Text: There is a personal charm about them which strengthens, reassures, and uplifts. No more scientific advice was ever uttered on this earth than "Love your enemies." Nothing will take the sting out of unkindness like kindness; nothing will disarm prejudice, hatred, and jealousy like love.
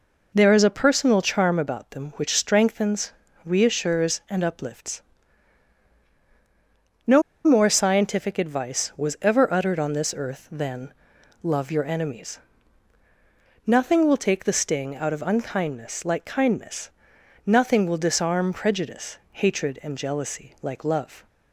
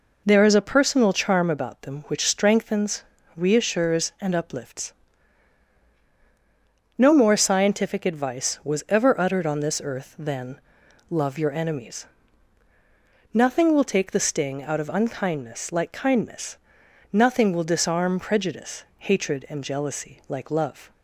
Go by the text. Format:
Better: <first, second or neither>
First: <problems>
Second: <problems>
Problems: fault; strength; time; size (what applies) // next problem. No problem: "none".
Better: second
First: pauses between "No" and "more"; slight; at 7.2 s; 0.23 s long // pauses between "than" and "Love"; noticeable; at 10.9 s; 0.48 s long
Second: pauses between "than" and "Love"; noticeable; at 10.6 s; 0.48 s long